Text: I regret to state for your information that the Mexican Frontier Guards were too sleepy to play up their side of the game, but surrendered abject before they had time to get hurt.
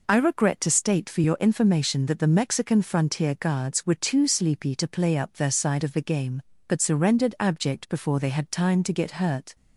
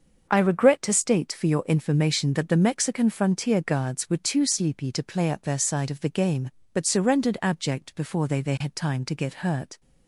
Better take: first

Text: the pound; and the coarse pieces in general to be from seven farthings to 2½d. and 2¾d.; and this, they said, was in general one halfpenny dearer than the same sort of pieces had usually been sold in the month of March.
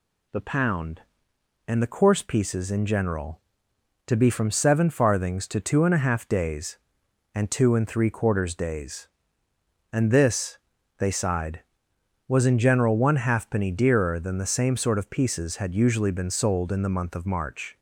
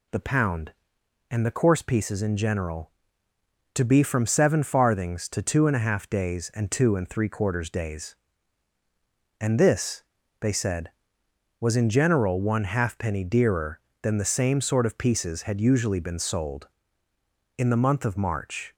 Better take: second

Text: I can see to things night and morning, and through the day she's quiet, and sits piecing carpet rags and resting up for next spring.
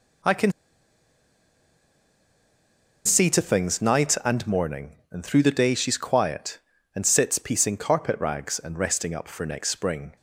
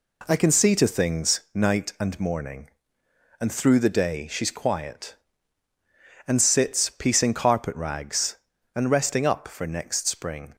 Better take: second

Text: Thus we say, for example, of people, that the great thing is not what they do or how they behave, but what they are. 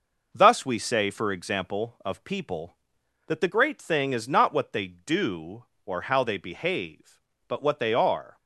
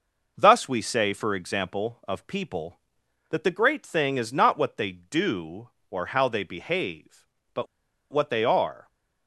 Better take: first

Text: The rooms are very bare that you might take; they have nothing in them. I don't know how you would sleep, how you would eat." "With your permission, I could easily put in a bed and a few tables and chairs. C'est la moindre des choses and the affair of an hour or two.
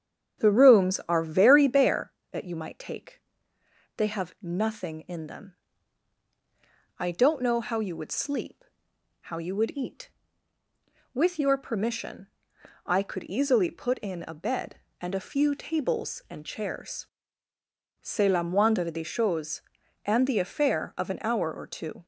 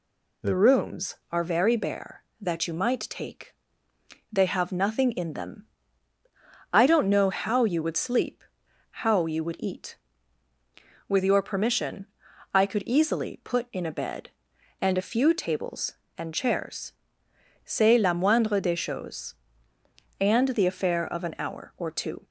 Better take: second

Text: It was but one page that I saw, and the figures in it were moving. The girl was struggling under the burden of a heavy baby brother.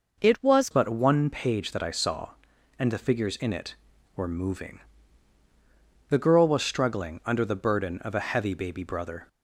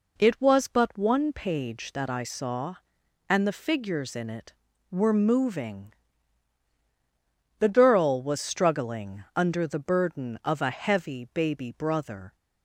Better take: second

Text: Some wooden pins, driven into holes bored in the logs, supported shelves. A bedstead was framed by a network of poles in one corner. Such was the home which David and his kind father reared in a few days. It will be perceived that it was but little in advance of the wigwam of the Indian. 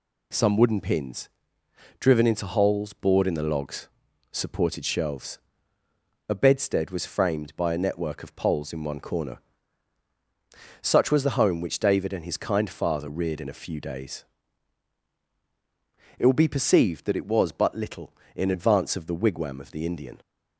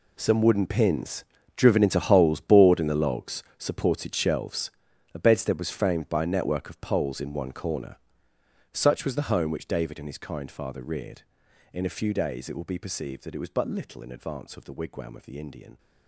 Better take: first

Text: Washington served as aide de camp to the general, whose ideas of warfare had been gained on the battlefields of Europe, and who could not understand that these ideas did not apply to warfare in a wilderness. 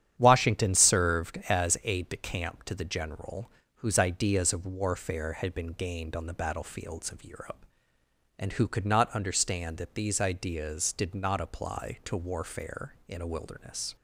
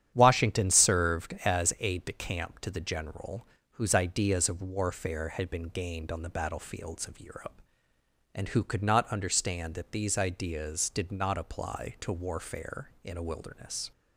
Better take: neither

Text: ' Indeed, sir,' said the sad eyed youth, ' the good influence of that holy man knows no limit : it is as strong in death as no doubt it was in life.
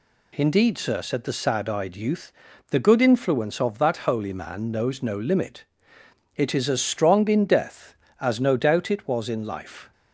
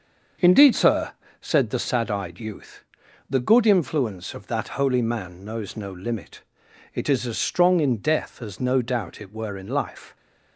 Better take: first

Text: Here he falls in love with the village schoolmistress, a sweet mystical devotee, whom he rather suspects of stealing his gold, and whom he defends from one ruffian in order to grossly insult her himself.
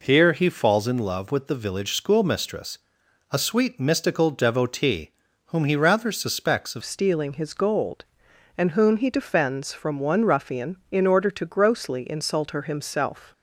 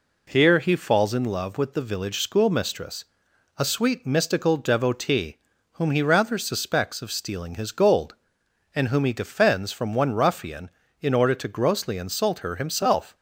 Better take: second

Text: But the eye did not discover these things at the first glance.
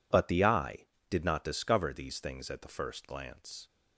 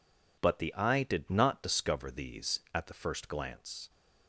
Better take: first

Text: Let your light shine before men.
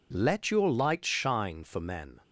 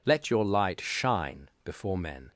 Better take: second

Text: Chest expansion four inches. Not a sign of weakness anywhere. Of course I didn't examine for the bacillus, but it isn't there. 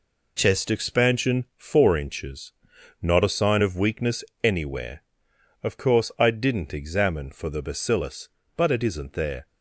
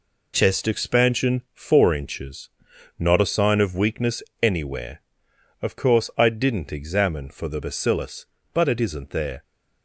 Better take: neither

